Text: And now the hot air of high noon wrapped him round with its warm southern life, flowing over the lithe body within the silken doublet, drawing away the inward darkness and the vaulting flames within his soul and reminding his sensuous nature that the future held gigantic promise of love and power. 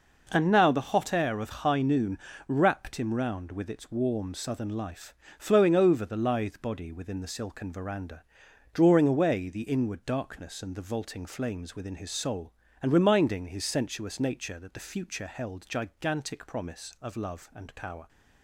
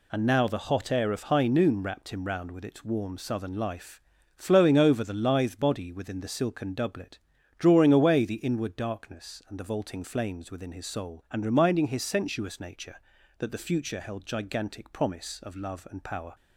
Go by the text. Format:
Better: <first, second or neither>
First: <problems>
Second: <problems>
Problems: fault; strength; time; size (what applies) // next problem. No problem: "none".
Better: second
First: pauses between "noon" and "wrapped"; slight; at 2.1 s; 0.30 s long // says "veranda" for "doublet"; at 7.7 s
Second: none